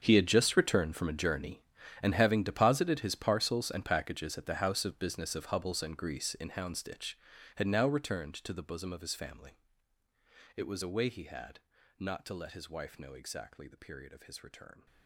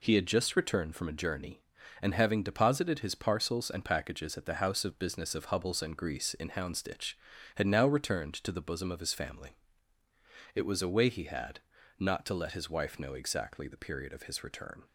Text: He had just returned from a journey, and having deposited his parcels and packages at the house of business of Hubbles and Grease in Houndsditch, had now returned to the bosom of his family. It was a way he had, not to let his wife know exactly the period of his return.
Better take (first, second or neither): second